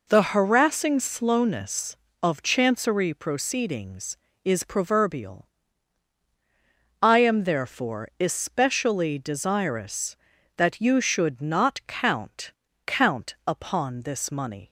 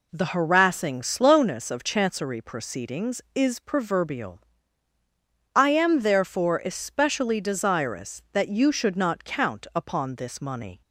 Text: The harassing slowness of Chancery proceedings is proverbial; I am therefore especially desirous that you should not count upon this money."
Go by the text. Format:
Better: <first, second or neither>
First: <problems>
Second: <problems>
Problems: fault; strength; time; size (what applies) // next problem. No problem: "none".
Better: second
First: says "count" twice; at 12.8 s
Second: none